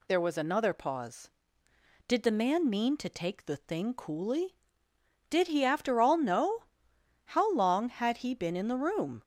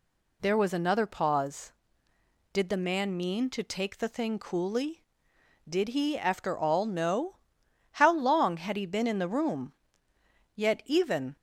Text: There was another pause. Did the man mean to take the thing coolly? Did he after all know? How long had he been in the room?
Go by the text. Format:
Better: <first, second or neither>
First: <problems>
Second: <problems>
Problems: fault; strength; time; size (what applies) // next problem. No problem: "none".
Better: first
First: none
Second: goes on to say "Yet even"; noticeable; from 10.5 s on; 0.80 s long